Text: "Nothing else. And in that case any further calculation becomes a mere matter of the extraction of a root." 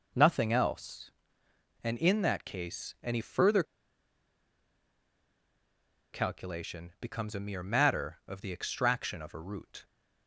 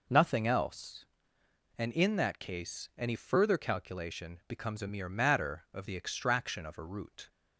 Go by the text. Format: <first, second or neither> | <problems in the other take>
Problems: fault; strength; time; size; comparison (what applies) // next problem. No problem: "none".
second | pauses between "further" and "calculation"; strong; at 3.6 s; 2.4 s long